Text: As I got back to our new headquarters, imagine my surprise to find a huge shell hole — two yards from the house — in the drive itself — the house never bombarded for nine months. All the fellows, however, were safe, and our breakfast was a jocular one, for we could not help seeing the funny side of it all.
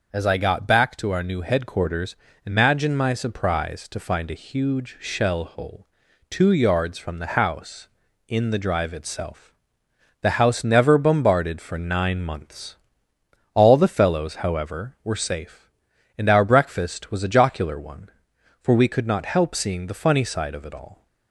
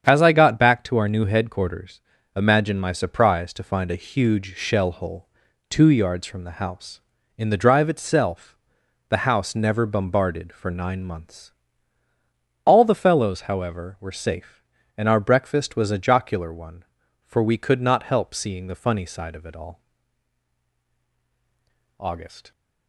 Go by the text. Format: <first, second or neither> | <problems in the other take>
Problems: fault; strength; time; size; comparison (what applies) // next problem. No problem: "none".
first | starts louder than the rest; strong; until 1.0 s; 8 dB // goes on to say "August"; from 21.9 s on; 0.52 s long